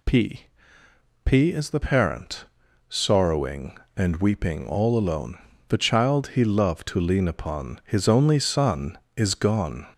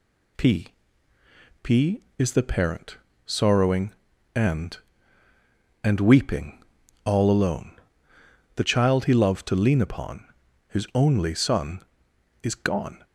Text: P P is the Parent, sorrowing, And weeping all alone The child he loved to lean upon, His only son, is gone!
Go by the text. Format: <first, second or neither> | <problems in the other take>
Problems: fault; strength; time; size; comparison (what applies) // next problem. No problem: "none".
first | pauses between "P" and "P"; noticeable; at 0.6 s; 0.96 s long; noticeable in the first // says "And" twice; at 5.8 s // pauses between "weeping" and "all"; at 6.5 s; 0.44 s long // pauses between "alone" and "The"; noticeable; at 7.7 s; 0.80 s long; slight in the first